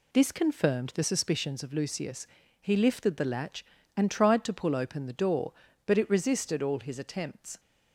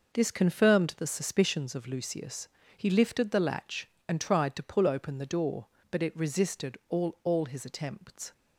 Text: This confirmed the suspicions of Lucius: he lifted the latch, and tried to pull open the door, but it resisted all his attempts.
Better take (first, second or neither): first